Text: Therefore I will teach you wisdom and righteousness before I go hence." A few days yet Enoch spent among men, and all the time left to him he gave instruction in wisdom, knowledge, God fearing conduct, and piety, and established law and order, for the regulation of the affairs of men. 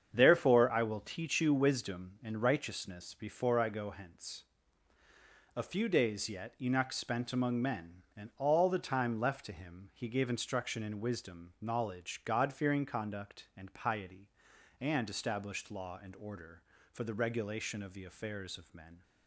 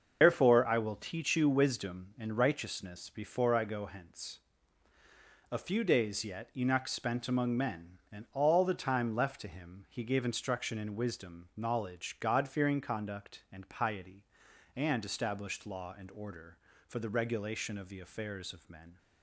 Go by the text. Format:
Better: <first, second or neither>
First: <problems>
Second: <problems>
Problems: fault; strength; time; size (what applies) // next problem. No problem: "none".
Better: first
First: starts louder than the rest; strong; until 1.1 s; 7.5 dB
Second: loses the start of "Therefore"; at 0.2 s; 125 ms // starts louder than the rest; until 1.2 s; 6.5 dB